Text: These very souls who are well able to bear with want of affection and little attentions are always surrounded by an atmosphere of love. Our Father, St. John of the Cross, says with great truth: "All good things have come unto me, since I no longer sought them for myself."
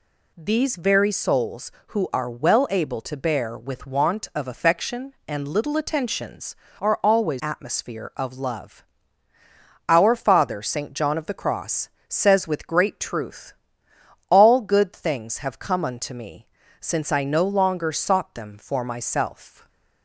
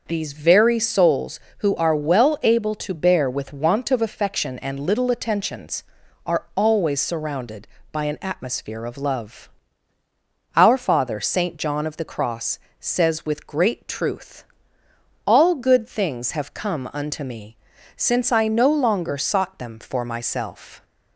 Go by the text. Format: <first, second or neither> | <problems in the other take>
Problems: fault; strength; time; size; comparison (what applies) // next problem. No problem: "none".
second | skips "surrounded by an"; at 7.4 s // stays silent after the last word; slight; from 19.4 s on; 0.6 s long